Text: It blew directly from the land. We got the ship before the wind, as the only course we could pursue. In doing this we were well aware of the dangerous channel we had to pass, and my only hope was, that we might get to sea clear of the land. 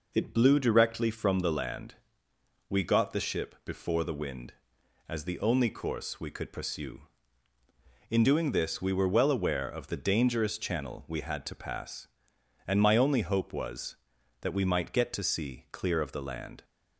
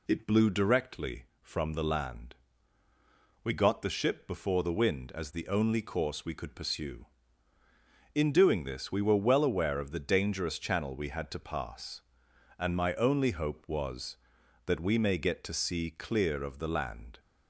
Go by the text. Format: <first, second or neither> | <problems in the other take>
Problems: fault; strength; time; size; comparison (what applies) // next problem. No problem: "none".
first | says "may" for "might"; at 14.9 s